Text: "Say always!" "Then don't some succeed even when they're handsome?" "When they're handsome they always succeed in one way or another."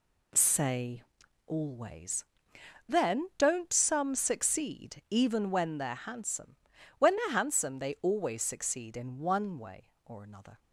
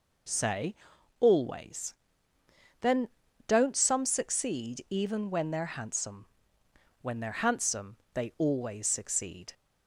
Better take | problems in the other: first | pauses between "Say" and "always"; noticeable; at 0.7 s; 0.46 s long; noticeable in the first // pauses between "Then" and "don't"; at 3.0 s; 0.40 s long // pauses between "handsome" and "they"; slight; at 7.9 s; 0.18 s long // stops before "in one way or another"; at 9.5 s

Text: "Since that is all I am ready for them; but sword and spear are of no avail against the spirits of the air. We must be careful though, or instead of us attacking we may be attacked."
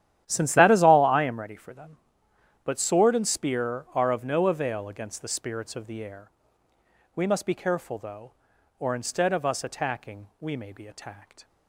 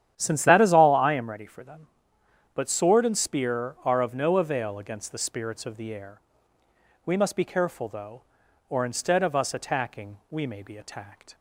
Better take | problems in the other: second | gets quieter; strong; throughout; 15 dB // starts louder than the rest; strong; until 1.2 s; 11.5 dB; strong in the second

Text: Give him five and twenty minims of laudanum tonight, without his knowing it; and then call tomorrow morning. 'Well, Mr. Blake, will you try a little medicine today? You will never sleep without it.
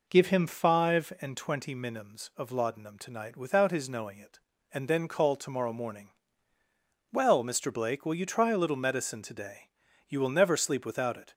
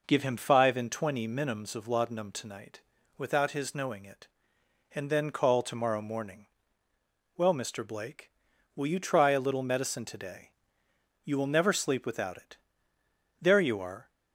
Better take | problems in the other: first | goes on to say "There you are"; noticeable; from 13.3 s on; 0.70 s long

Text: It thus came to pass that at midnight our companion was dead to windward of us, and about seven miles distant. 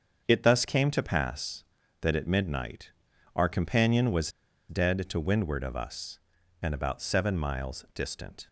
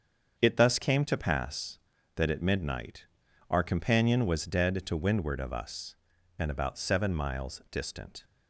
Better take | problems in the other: second | starts louder than the rest; until 1.2 s; 7 dB; also in the second // pauses between "midnight" and "our"; at 2.9 s; 0.44 s long; also in the second // pauses between "was" and "dead"; at 4.3 s; 0.38 s long

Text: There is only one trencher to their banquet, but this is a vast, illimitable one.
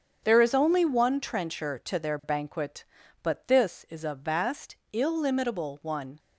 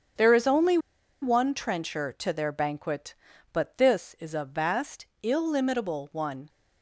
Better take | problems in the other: first | starts louder than the rest; strong; until 1.6 s; 7.5 dB; strong in the first // pauses between "only" and "one"; at 0.7 s; 0.44 s long

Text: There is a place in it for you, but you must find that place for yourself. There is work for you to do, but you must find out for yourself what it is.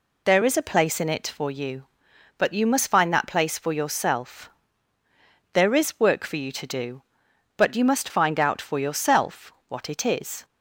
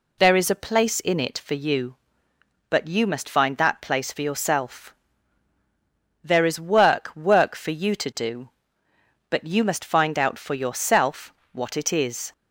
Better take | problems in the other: first | says "work" twice; at 7.1 s // pauses between "yourself" and "what"; slight; at 11.3 s; 0.18 s long; slight in the first

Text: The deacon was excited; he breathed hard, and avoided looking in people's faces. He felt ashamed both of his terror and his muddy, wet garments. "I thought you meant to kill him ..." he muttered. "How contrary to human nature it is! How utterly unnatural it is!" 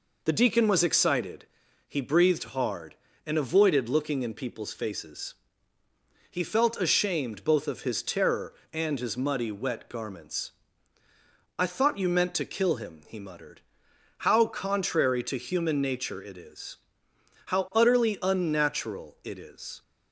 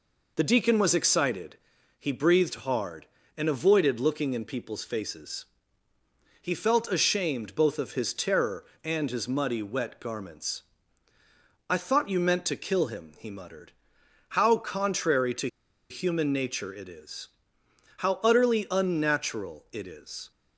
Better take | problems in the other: first | pauses between "to" and "human"; at 15.4 s; 0.42 s long

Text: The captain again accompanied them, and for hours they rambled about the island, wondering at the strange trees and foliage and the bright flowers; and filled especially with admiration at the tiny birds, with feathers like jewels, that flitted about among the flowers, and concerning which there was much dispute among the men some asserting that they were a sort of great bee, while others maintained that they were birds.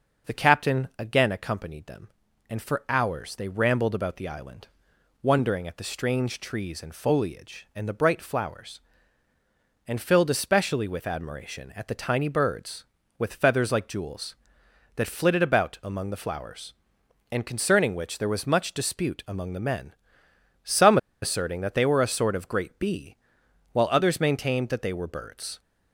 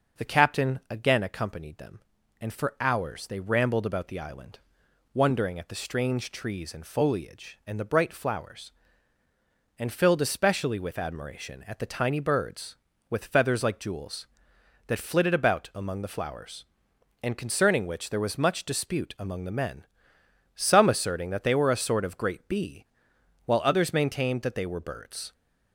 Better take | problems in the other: second | starts louder than the rest; until 1.3 s; 6.5 dB; also in the second // pauses between "men" and "some"; noticeable; at 19.9 s; 0.74 s long; noticeable in the second // pauses between "some" and "asserting"; slight; at 20.9 s; 0.24 s long

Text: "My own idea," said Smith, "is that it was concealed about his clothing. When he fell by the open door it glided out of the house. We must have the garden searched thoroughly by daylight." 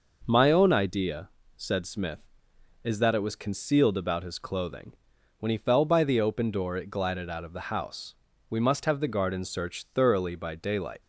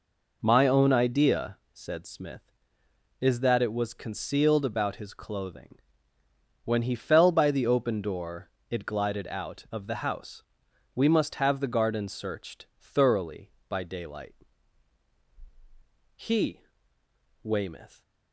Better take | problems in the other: first | pauses between "door" and "it"; slight; at 8.4 s; 0.20 s long // goes on to say "He Weymouth"; strong; from 16.1 s on; 1.8 s long

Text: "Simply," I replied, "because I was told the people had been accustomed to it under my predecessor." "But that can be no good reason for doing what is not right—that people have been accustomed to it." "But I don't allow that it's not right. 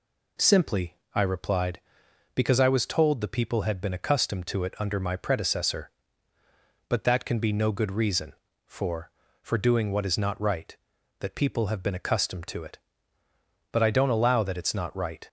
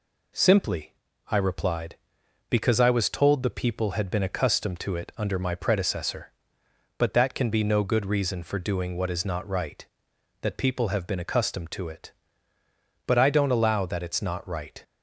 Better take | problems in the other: second | says "for" twice; at 9.4 s

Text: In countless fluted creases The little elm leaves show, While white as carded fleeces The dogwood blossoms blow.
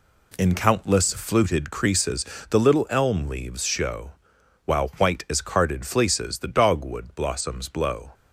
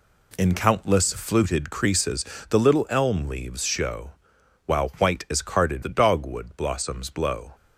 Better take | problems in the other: first | pauses between "creases" and "The"; slight; at 2.2 s; 0.24 s long; slight in the first // skips "fleeces"; at 5.8 s

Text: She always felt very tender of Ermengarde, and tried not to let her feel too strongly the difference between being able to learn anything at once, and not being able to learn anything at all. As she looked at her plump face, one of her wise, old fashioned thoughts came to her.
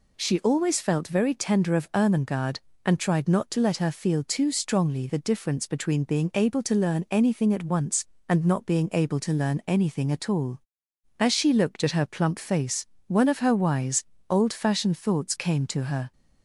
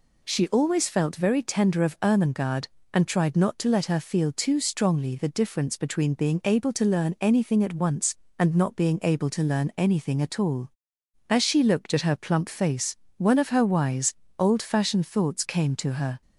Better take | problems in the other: neither | none

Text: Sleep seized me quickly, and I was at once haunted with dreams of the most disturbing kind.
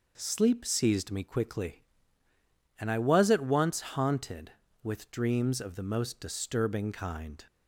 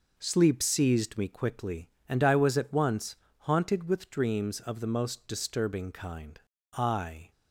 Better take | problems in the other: first | pauses between "once" and "haunted"; slight; at 3.1 s; 0.22 s long // goes on to say "I"; from 6.7 s on; 0.58 s long

